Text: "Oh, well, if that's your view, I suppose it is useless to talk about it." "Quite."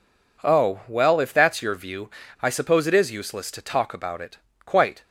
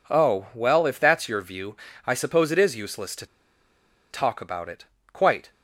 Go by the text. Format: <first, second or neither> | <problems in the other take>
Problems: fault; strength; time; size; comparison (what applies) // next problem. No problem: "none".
first | pauses between "to" and "talk"; noticeable; at 3.2 s; 0.85 s long